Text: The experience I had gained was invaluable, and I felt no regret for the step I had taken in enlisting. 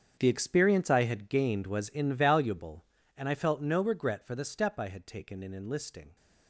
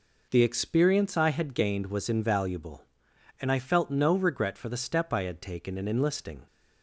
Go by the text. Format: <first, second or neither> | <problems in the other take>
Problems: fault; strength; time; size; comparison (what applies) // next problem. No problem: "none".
second | gets quieter; strong; throughout; 14.5 dB